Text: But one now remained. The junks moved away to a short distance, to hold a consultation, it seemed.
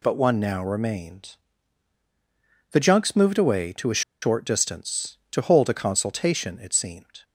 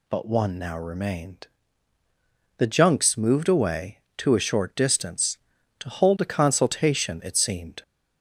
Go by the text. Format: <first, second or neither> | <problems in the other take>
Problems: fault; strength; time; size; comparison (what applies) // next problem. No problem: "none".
second | pauses between "a" and "short"; slight; at 4.0 s; 0.21 s long